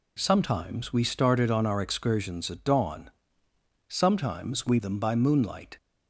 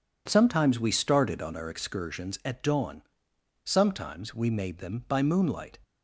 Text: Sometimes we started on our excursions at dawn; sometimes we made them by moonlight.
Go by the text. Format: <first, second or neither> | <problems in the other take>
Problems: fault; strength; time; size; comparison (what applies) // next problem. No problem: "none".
second | skips "made"; at 4.8 s